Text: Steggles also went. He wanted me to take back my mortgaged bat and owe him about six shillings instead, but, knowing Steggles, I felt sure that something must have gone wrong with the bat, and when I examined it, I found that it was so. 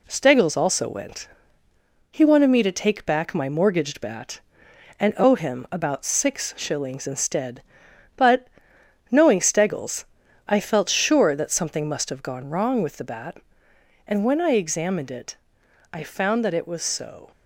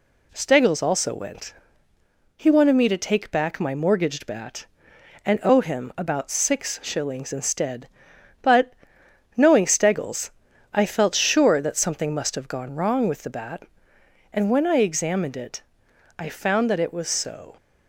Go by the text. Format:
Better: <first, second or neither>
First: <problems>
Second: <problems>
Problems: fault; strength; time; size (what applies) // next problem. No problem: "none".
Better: second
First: gets quieter; throughout; 3.5 dB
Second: none